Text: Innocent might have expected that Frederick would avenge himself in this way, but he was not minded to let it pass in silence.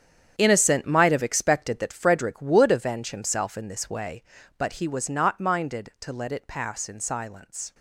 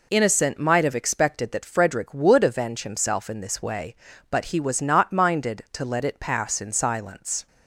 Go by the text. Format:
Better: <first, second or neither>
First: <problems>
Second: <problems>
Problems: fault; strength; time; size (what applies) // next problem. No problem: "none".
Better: second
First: gets quieter; strong; throughout; 12.5 dB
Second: none